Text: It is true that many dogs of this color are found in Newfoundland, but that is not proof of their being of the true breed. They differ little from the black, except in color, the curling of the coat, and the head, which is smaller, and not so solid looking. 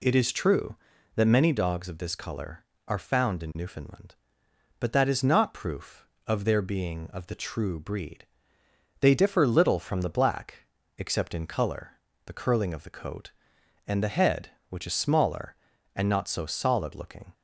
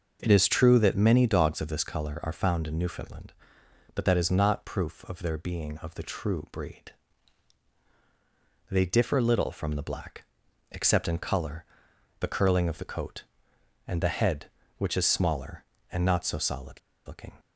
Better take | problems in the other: first | pauses between "solid" and "looking"; slight; at 16.7 s; 0.28 s long

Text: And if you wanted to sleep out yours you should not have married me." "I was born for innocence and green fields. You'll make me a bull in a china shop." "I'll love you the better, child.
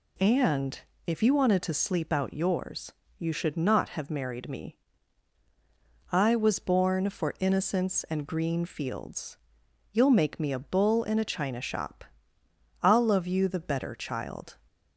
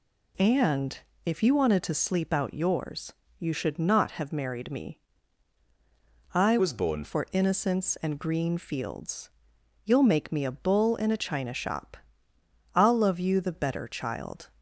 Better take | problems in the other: first | pauses between "And" and "if"; slight; at 0.9 s; 0.26 s long; slight in the first // pauses between "yours" and "you"; slight; at 3.1 s; 0.26 s long; slight in the first // changes voice from "was" to "born"; from 6.5 to 7.0 s; 0.5 s long

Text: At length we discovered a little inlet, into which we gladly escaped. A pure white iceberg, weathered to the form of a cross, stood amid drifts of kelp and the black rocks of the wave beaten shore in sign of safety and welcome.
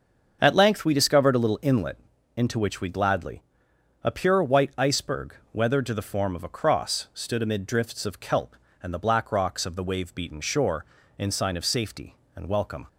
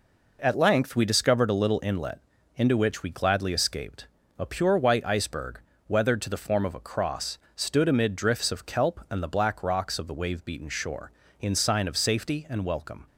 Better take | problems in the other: second | starts louder than the rest; until 1.4 s; 7 dB // skips "escaped"; at 3.7 s

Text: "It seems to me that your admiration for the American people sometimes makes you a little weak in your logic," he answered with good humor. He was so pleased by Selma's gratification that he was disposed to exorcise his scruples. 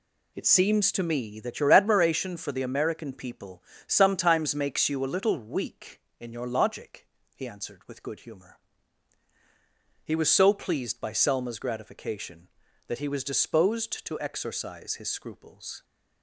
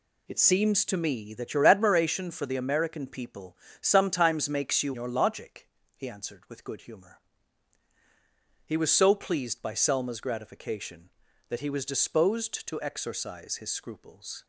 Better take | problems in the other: first | pauses between "people" and "sometimes"; slight; at 3.5 s; 0.24 s long; slight in the first // skips "a little weak in"; at 4.9 s

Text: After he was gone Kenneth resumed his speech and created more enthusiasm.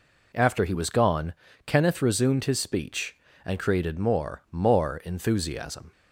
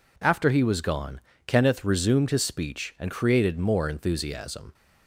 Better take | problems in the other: second | pauses between "gone" and "Kenneth"; slight; at 1.3 s; 0.32 s long; slight in the second // says "more" twice; at 4.5 s

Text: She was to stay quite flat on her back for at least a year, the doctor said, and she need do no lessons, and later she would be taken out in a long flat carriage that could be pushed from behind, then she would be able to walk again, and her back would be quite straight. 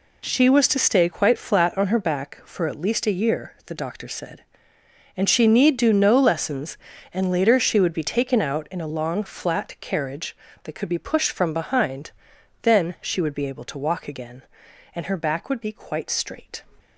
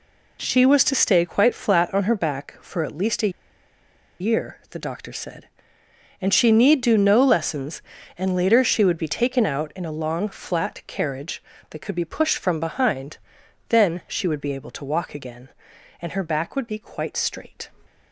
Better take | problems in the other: first | pauses between "a" and "year"; noticeable; at 3.3 s; 0.89 s long

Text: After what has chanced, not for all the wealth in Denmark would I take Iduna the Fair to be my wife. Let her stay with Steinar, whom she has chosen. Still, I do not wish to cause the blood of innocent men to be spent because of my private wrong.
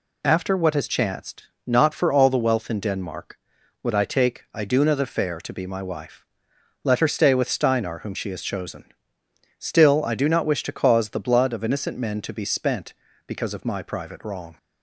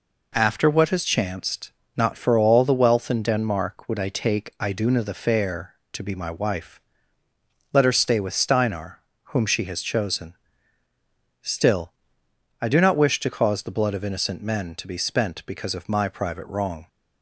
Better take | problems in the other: neither | none

